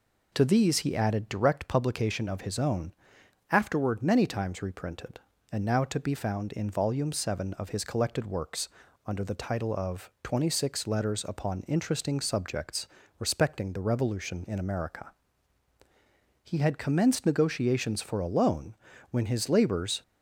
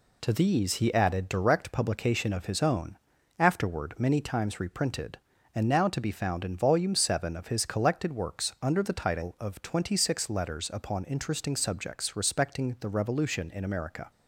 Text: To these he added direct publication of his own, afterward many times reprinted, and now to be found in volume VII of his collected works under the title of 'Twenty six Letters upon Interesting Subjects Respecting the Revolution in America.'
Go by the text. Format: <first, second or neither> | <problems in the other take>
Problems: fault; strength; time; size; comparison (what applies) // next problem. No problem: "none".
second | pauses between "works" and "under"; slight; at 8.6 s; 0.36 s long // pauses between "Subjects" and "Respecting"; slight; at 12.8 s; 0.32 s long // goes on to say "He had commenced negotiations for a loan when his labors"; strong; from 16.4 s on; 3.5 s long